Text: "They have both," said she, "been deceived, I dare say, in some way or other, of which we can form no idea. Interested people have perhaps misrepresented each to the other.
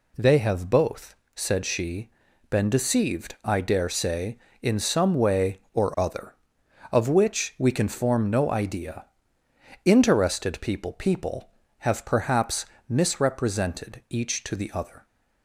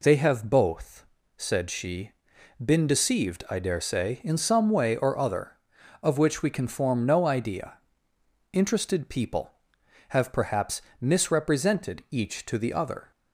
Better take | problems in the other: second | says "people" twice; at 10.9 s // pauses between "perhaps" and "misrepresented"; slight; at 12.6 s; 0.24 s long; slight in the second

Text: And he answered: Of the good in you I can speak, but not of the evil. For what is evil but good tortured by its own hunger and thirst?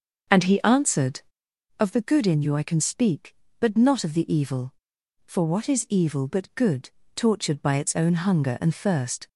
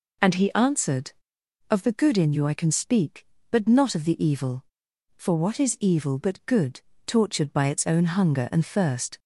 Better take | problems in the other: second | starts louder than the rest; until 1.6 s; 6.5 dB // pauses between "good" and "tortured"; slight; at 6.8 s; 0.26 s long; slight in the second

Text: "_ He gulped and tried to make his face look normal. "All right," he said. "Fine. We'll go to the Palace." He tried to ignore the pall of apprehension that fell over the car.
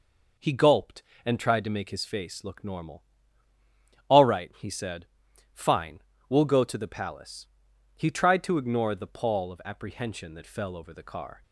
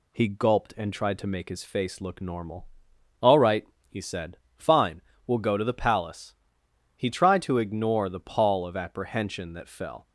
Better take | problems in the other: first | stops before "over the car"; at 10.0 s

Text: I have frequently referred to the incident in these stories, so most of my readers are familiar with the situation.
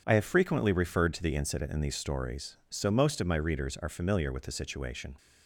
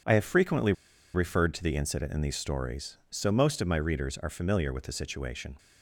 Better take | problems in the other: first | pauses between "frequently" and "referred"; at 0.7 s; 0.40 s long

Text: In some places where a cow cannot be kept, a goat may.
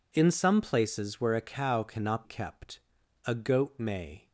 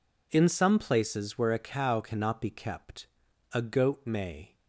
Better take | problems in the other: second | skips "be"; at 2.2 s

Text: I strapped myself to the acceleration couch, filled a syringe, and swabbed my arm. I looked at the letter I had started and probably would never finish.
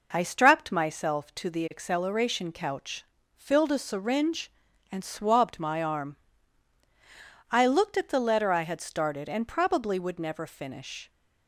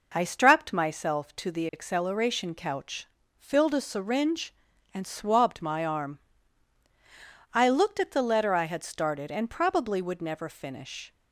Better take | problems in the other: neither | none

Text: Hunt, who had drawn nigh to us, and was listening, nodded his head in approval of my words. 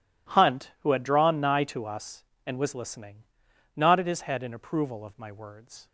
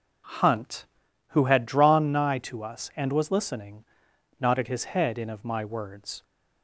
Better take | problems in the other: first | skips "approval"; at 5.2 s

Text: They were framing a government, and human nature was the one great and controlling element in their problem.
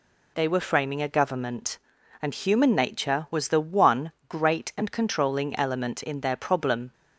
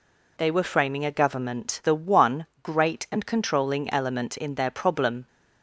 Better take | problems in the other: first | skips "and human nature was"; at 1.8 s // pauses between "one" and "great"; slight; at 2.4 s; 0.16 s long; slight in the first

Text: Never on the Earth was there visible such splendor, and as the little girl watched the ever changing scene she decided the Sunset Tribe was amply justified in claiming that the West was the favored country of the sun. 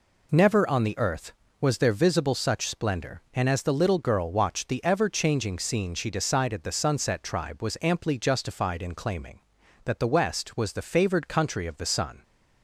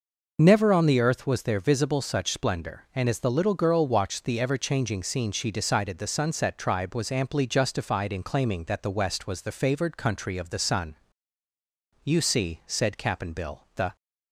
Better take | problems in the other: first | goes on to say "You see said Cap'n Bill the"; strong; from 12.0 s on; 1.9 s long

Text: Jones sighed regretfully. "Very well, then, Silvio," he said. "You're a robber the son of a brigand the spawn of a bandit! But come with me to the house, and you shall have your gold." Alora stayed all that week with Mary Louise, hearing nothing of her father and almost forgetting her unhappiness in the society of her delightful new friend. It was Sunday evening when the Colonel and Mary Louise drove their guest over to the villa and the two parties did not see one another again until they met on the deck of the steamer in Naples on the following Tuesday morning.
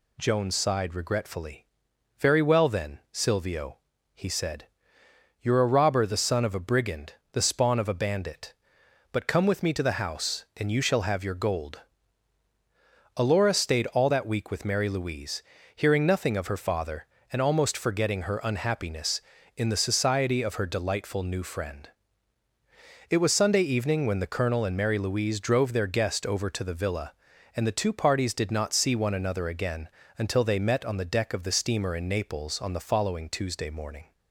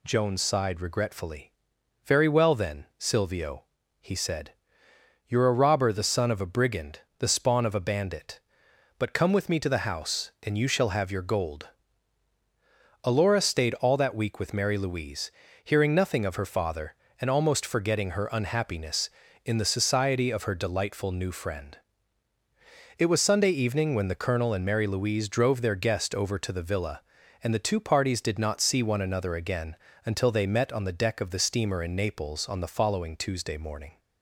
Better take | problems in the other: neither | pauses between "brigand" and "the"; slight; the same in both // pauses between "again" and "until"; slight; the same in both

